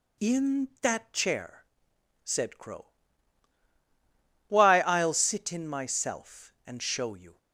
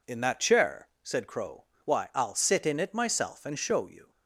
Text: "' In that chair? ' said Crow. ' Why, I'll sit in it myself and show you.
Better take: second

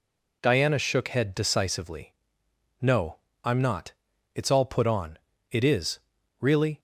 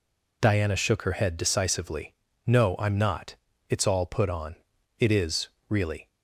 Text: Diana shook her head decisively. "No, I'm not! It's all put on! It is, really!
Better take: second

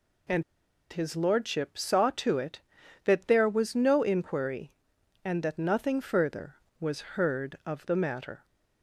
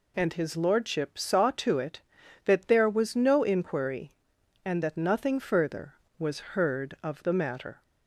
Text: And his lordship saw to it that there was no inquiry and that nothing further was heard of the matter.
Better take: second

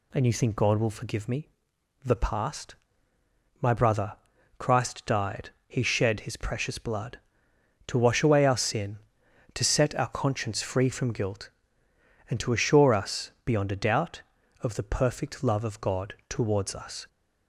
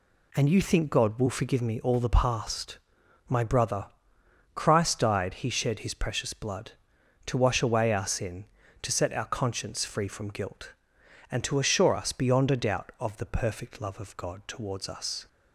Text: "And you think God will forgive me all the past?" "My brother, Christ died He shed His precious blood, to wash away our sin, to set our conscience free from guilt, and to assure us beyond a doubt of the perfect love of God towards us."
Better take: second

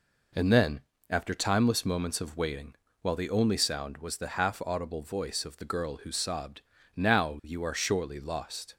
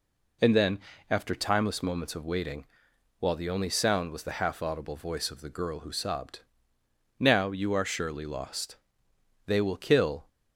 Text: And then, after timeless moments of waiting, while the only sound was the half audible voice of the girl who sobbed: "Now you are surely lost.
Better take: first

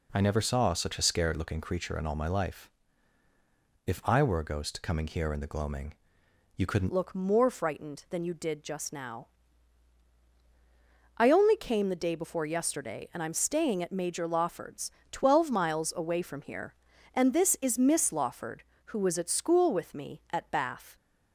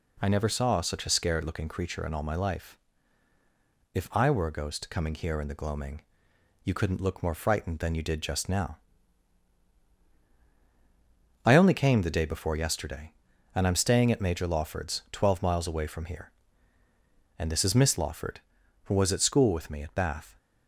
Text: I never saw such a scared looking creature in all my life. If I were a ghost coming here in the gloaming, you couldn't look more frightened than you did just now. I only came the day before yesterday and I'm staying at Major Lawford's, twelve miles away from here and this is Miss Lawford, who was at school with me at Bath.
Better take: second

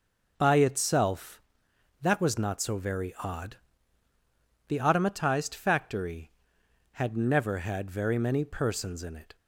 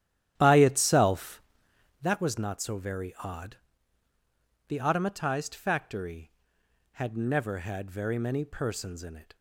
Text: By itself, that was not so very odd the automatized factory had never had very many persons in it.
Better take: first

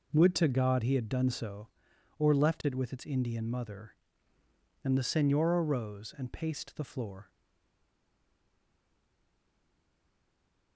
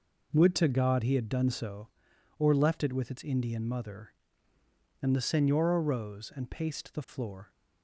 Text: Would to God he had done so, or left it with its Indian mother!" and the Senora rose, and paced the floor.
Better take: second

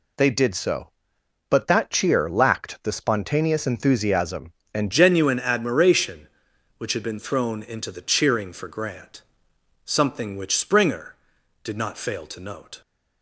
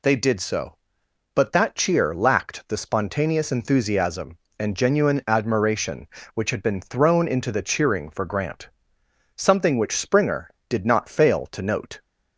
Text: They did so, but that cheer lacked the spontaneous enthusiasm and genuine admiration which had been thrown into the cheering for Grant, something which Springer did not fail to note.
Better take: second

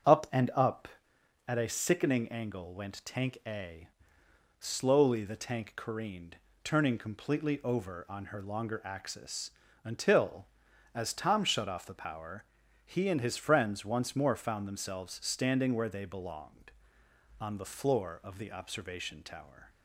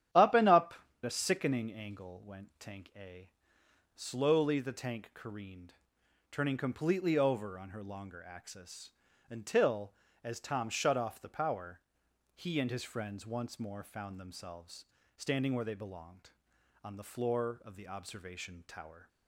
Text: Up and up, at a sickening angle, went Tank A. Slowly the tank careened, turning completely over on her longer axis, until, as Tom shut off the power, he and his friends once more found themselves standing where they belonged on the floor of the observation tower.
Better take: first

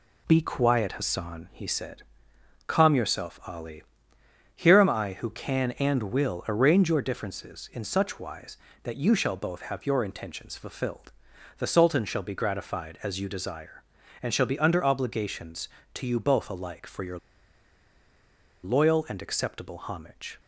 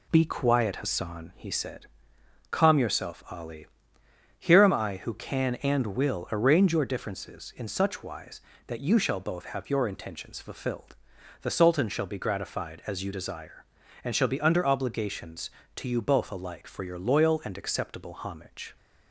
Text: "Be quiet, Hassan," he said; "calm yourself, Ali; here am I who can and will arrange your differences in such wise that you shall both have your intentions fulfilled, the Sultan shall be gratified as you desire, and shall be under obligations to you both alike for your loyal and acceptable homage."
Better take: second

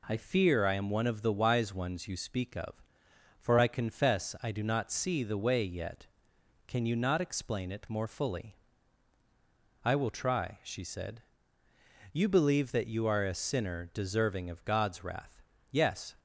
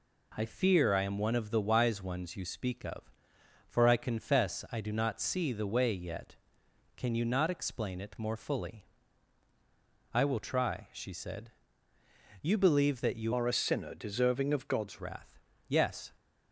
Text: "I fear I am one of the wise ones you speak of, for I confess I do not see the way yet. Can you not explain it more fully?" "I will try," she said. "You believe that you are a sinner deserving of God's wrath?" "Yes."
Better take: first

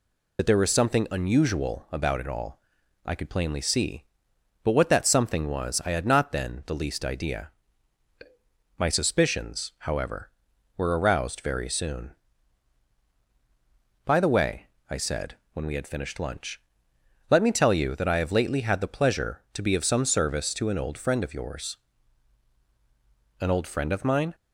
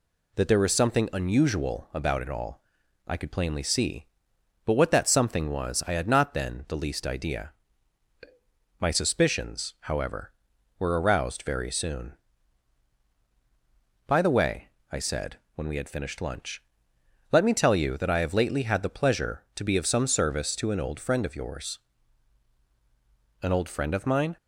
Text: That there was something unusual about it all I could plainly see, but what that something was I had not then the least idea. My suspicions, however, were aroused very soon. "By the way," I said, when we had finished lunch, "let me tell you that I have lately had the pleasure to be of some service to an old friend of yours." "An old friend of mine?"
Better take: second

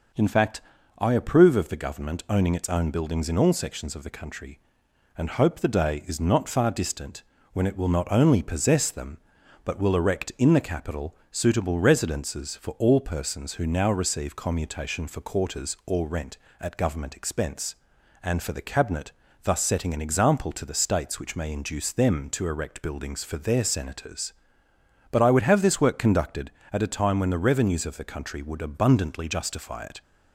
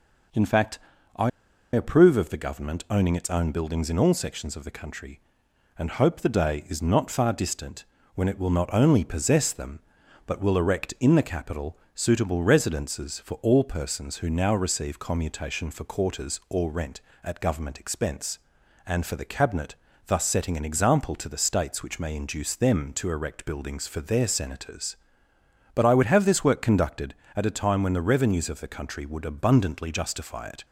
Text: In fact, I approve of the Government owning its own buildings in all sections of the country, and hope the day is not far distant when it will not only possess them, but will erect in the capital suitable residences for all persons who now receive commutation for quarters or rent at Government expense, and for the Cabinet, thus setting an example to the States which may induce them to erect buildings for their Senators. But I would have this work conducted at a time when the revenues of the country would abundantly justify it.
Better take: first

